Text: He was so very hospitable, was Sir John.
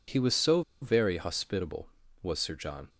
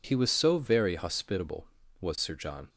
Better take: second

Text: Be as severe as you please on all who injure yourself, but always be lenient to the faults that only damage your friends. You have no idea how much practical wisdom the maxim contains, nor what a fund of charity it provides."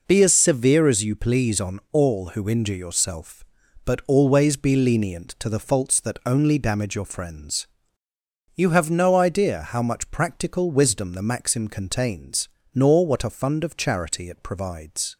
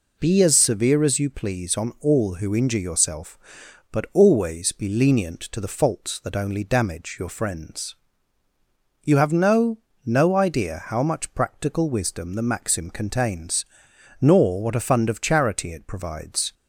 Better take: first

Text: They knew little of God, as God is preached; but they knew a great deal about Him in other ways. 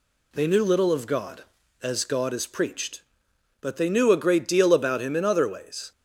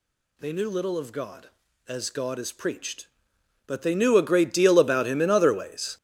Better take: first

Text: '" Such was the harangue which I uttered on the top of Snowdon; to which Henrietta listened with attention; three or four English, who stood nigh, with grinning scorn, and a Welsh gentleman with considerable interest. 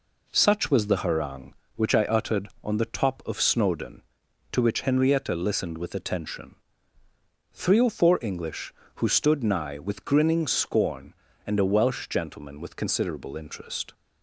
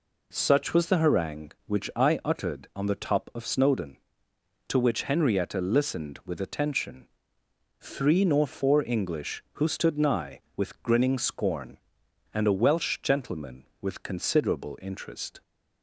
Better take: first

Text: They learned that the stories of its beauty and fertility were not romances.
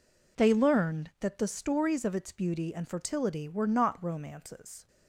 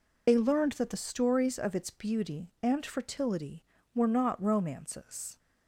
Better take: first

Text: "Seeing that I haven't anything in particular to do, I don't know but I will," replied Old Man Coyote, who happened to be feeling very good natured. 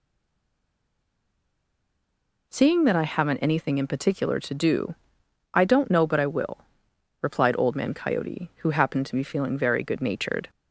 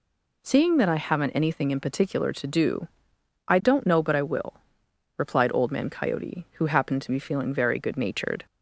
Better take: second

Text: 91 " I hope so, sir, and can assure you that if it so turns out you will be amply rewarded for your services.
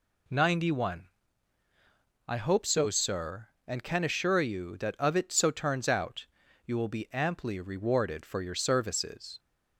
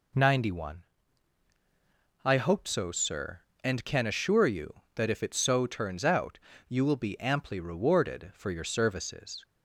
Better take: second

